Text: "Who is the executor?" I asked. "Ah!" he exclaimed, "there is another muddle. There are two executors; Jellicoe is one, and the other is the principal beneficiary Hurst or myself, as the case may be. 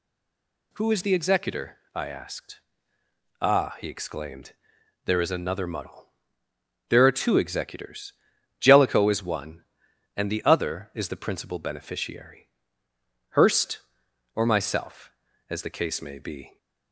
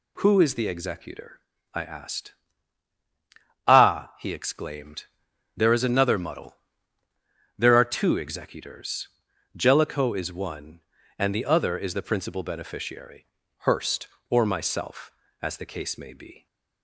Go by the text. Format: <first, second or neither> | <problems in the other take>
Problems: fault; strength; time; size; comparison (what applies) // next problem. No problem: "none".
second | stays silent before the first word; slight; until 0.7 s; 0.7 s long // pauses between "beneficiary" and "Hurst"; noticeable; at 12.4 s; 0.80 s long; also in the second